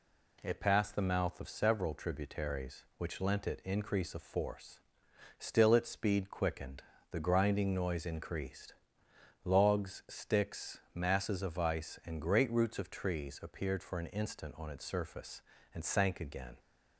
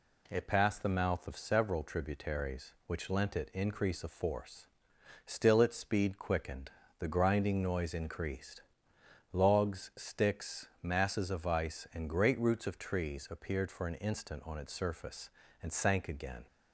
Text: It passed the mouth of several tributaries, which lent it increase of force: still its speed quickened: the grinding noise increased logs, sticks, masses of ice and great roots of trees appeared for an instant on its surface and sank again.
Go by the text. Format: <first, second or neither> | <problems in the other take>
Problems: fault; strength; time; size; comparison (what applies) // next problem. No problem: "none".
neither | pauses between "increased" and "logs"; noticeable; the same in both